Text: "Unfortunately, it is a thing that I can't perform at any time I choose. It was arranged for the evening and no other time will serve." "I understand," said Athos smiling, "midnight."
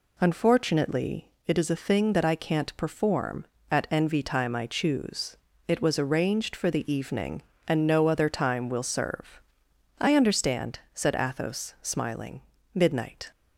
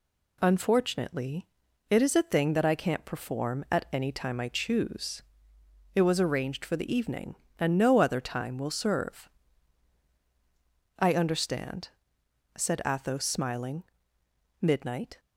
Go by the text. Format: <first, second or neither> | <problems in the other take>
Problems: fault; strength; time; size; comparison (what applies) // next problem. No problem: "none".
second | says "envy" for "any"; at 3.8 s